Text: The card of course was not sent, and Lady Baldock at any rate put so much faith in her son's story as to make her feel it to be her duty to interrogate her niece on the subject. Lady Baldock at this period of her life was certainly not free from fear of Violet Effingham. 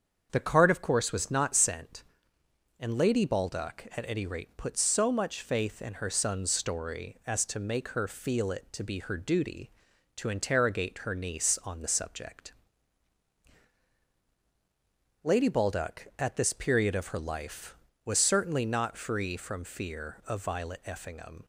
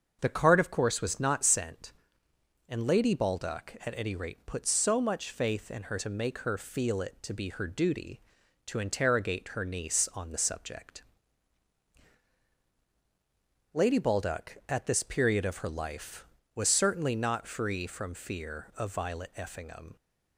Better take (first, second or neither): first